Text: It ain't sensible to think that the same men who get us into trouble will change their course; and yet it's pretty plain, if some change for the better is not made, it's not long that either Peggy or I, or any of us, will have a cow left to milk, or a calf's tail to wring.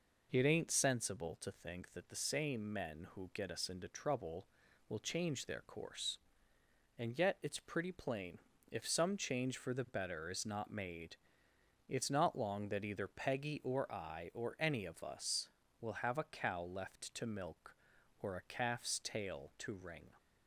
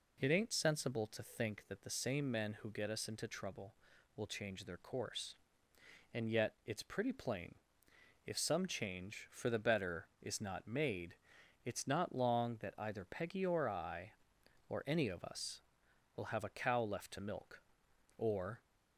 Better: first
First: none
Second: stops before "a calf's tail to wring"; at 18.6 s

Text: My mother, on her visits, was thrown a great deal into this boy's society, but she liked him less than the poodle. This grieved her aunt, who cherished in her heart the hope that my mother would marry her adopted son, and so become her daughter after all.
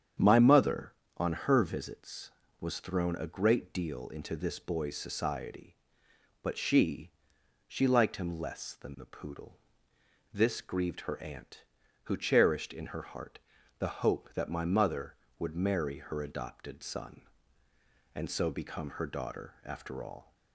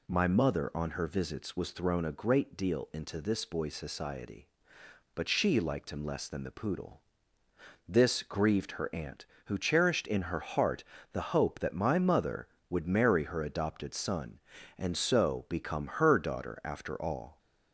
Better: second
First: starts louder than the rest; strong; until 1.4 s; 8.5 dB // says "she" twice; at 7.6 s // pauses between "heart" and "the"; at 13.3 s; 0.40 s long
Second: pauses between "heart" and "the"; slight; at 10.8 s; 0.30 s long

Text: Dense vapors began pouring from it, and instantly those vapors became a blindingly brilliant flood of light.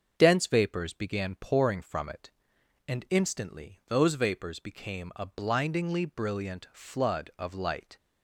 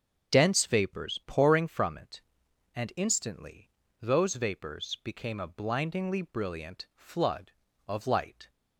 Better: first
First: starts louder than the rest; until 1.1 s; 6.5 dB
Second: starts louder than the rest; until 1.3 s; 7 dB // skips "began"; at 1.2 s // pauses between "instantly" and "those"; slight; at 3.7 s; 0.28 s long

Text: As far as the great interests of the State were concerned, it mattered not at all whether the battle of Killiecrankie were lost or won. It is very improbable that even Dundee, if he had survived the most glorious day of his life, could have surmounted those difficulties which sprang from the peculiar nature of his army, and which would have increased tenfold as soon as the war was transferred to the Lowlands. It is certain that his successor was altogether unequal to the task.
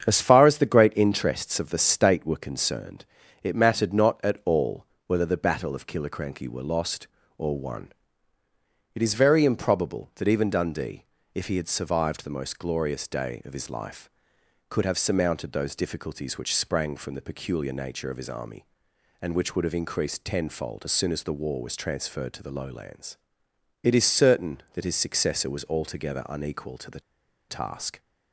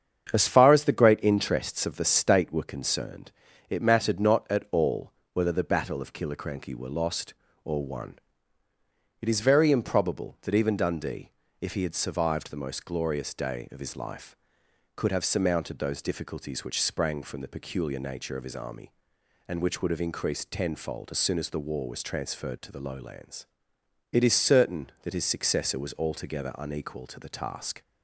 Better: second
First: starts louder than the rest; strong; until 1.1 s; 8 dB // pauses between "all" and "whether"; slight; at 4.8 s; 0.18 s long // pauses between "the" and "task"; noticeable; at 27.0 s; 0.47 s long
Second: starts louder than the rest; strong; until 1.3 s; 8 dB // pauses between "all" and "whether"; slight; at 5.1 s; 0.18 s long

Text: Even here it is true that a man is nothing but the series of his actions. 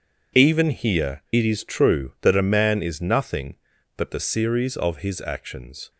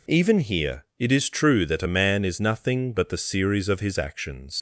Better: first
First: none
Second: leaves "actions" unfinished; at 4.5 s; 100 ms

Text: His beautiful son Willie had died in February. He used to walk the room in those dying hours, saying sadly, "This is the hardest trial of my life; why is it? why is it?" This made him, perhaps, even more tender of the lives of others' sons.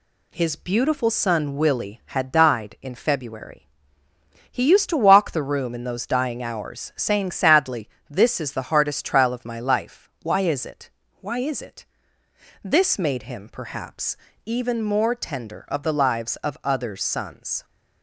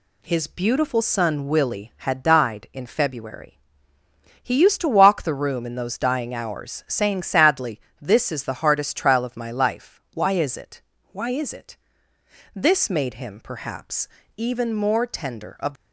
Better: first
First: none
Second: stops before "the lives of others sons"; at 15.7 s

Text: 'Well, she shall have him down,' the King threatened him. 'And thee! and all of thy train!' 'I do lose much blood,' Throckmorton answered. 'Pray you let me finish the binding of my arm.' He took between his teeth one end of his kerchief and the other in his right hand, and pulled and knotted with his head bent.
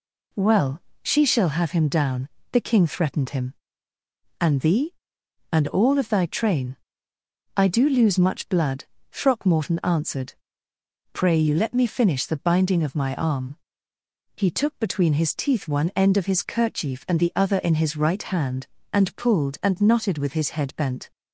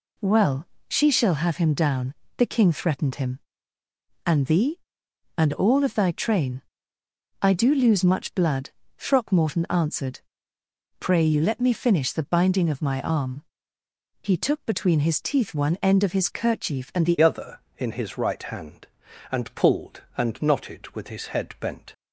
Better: first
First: none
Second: changes voice at "other"; from 17.2 s on; 4.7 s long

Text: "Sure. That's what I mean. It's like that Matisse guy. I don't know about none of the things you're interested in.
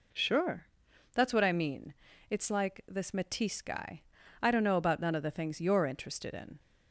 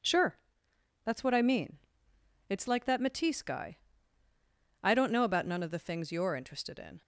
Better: second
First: says "this" for "that"; at 2.8 s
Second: none

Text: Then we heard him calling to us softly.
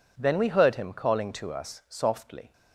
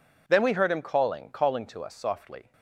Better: first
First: none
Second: says "calling" twice; at 1.3 s

